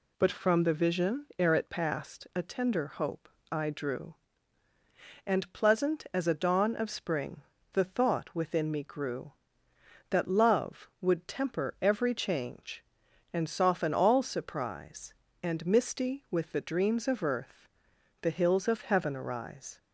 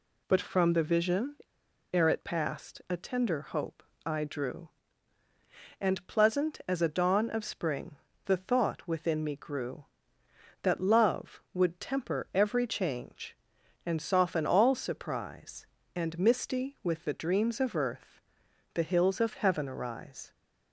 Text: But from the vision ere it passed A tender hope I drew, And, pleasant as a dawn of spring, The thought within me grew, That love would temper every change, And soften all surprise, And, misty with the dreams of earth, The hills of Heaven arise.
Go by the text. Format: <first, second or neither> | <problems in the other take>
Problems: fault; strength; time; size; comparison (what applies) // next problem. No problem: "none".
first | pauses between "vision" and "ere"; noticeable; at 1.3 s; 0.58 s long // pauses between "hope" and "I"; slight; at 3.8 s; 0.22 s long; slight in the first